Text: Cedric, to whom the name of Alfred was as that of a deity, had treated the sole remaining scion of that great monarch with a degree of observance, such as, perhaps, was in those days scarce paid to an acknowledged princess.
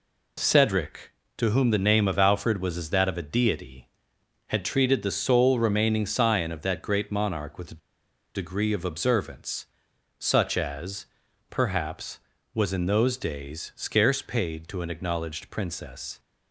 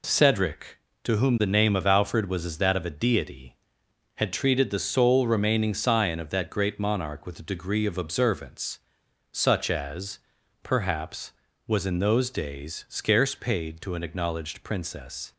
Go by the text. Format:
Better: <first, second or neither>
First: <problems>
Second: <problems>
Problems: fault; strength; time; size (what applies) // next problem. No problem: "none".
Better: second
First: pauses between "a" and "degree"; noticeable; at 7.7 s; 0.55 s long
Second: none